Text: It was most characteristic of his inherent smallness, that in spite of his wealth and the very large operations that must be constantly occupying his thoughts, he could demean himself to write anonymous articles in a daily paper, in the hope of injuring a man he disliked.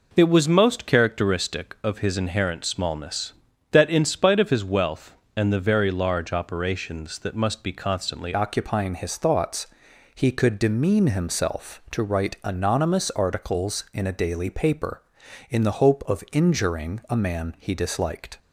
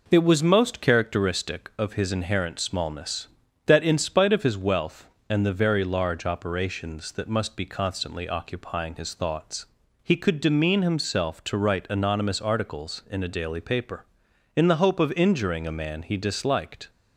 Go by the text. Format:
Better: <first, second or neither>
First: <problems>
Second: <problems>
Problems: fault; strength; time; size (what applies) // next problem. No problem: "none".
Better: second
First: changes voice at "occupying"; from 8.3 s on; 10.0 s long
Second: none